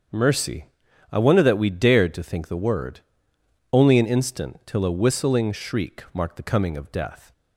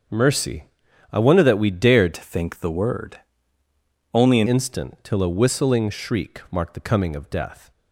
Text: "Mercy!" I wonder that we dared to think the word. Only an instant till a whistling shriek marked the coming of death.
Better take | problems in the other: first | starts louder than the rest; strong; until 1.5 s; 7.5 dB; strong in the first // changes voice from "to" to "an"; from 2.1 to 4.4 s; 2.3 s long

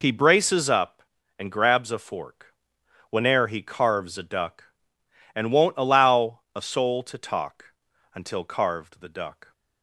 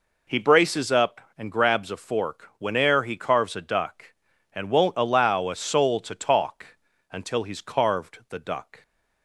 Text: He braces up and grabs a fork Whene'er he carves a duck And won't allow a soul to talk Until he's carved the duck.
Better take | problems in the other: second | pauses between "fork" and "Whene'er"; noticeable; at 2.5 s; 0.56 s long // pauses between "allow" and "a"; slight; at 6.3 s; 0.16 s long // pauses between "talk" and "Until"; noticeable; at 7.6 s; 0.46 s long; slight in the second // skips "he's"; at 8.4 s

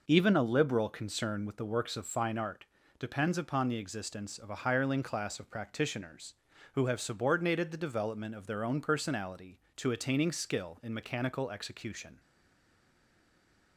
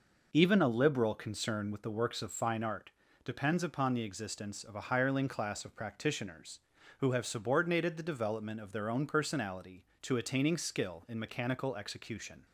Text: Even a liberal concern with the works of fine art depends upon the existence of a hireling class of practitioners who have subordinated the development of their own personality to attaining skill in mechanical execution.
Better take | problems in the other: second | pauses between "art" and "depends"; slight; at 2.6 s; 0.34 s long; slight in the second // stays silent after the last word; noticeable; from 12.1 s on; 1.6 s long

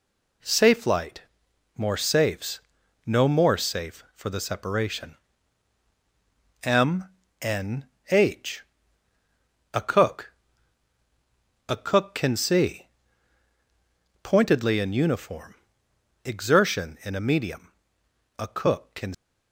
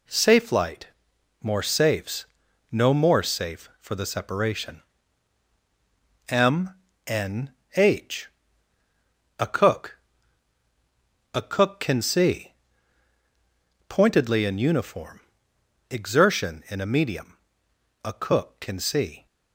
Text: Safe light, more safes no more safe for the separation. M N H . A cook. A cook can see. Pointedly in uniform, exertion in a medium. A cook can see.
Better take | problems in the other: second | pauses between "safes" and "no"; noticeable; at 2.5 s; 0.46 s long; noticeable in the second // pauses between "M" and "N"; slight; at 7.0 s; 0.34 s long; slight in the second // pauses between "N" and "H"; slight; at 7.8 s; 0.26 s long; slight in the second // stops before "see"; at 19.1 s

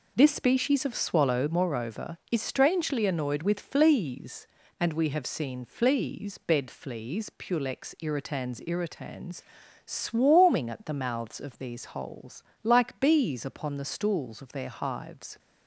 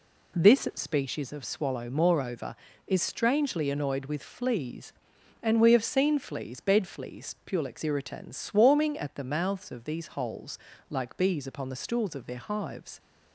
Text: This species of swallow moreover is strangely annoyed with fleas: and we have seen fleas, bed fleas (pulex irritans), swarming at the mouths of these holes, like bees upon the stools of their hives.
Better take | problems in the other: second | says "irritans" twice; at 8.6 s

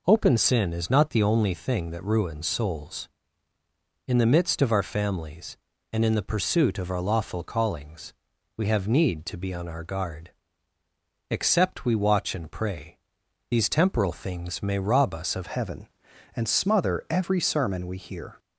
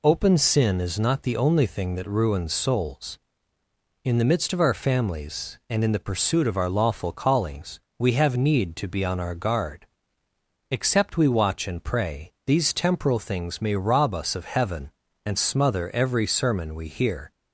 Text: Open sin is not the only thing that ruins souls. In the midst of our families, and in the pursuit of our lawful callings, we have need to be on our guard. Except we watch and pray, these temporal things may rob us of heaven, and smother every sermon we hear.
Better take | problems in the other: second | changes voice at "heaven"; from 15.4 s on; 2.9 s long

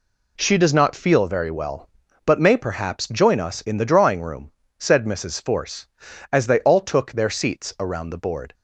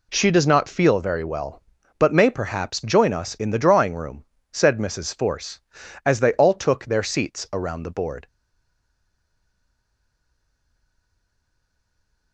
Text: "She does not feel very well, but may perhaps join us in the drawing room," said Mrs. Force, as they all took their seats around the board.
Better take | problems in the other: first | stays silent after the last word; strong; from 8.2 s on; 4.1 s long

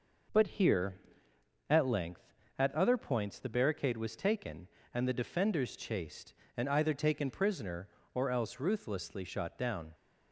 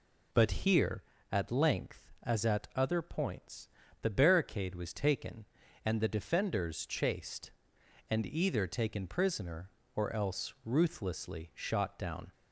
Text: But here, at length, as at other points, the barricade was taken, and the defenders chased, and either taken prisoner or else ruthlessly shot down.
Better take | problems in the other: second | skips "as"; at 2.4 s

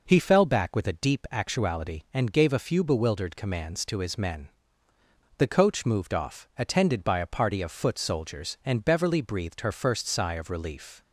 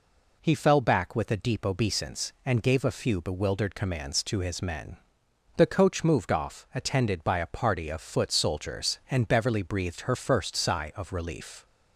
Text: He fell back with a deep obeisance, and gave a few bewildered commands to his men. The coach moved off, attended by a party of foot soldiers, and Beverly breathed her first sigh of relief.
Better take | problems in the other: second | says "actuality" for "obeisance"; at 1.3 s

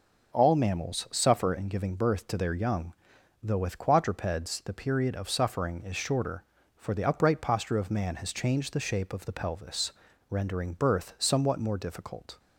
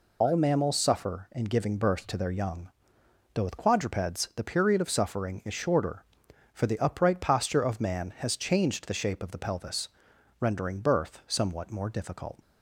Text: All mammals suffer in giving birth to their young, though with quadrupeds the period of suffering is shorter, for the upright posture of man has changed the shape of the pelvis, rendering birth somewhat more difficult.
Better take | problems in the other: first | loses the start of "All"; at 0.2 s; 65 ms

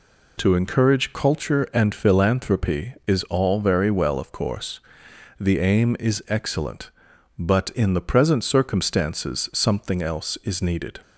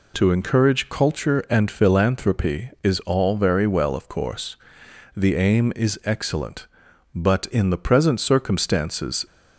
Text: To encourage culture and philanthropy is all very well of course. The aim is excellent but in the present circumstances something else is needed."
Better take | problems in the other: first | stops before "something else is needed"; at 9.2 s

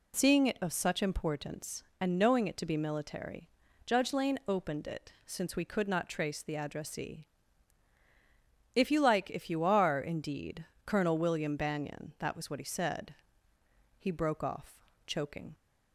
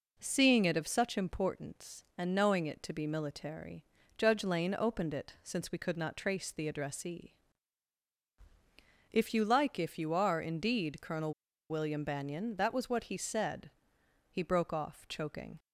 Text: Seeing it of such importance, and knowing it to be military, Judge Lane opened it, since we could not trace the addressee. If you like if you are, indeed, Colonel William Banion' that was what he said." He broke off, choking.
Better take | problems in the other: first | pauses between "Colonel" and "William"; at 11.3 s; 0.37 s long

